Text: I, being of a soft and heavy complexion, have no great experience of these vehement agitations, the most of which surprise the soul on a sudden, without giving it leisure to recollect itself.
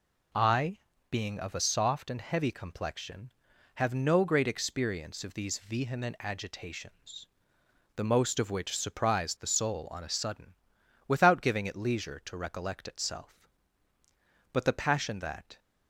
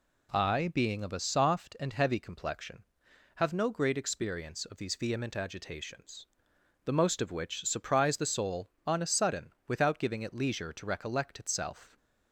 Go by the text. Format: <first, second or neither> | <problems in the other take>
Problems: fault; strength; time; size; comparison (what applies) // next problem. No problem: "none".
second | goes on to say "But the passion that"; noticeable; from 14.5 s on; 1.0 s long